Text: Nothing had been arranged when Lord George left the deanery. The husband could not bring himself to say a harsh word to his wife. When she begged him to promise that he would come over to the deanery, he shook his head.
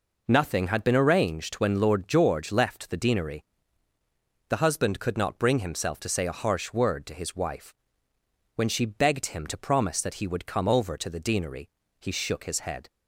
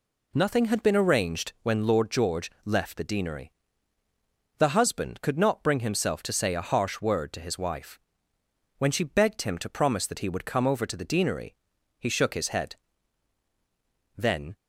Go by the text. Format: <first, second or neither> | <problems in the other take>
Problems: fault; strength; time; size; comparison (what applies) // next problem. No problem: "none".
first | goes on to say "Then"; slight; from 14.1 s on; 0.38 s long